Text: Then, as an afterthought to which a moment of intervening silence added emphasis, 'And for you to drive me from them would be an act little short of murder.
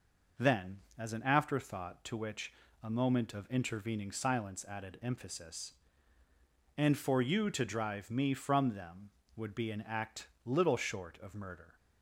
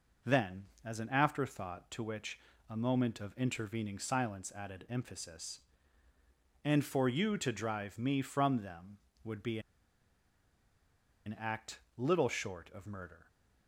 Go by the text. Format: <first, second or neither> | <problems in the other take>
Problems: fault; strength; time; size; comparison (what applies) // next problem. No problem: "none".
first | pauses between "which" and "a"; slight; at 2.3 s; 0.30 s long; slight in the first // pauses between "be" and "an"; strong; at 9.5 s; 1.6 s long // pauses between "act" and "little"; slight; at 11.7 s; 0.18 s long; slight in the first